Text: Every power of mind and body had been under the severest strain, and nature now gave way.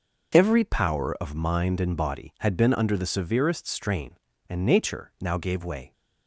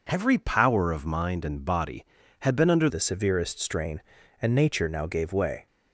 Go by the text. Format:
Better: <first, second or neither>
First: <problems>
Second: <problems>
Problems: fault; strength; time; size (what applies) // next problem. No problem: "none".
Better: first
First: none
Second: changes voice at "the"; from 2.8 s on; 2.8 s long